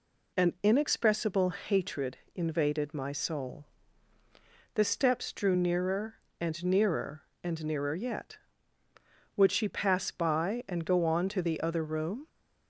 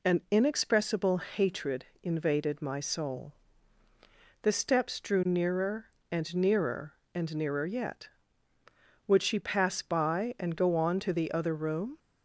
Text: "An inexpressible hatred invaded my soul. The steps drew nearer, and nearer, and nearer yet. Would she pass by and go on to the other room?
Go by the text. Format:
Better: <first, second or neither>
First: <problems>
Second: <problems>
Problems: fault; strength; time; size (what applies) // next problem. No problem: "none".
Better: neither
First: pauses between "hatred" and "invaded"; slight; at 2.1 s; 0.18 s long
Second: pauses between "hatred" and "invaded"; slight; at 1.8 s; 0.18 s long